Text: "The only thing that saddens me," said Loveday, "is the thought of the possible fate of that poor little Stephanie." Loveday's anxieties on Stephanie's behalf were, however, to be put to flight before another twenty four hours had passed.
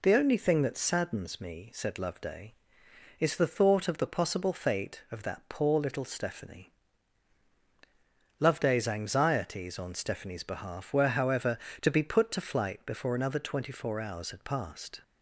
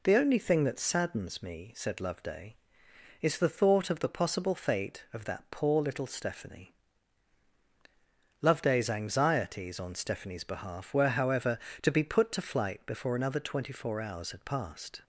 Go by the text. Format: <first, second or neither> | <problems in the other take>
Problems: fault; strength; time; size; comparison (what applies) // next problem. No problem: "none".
neither | none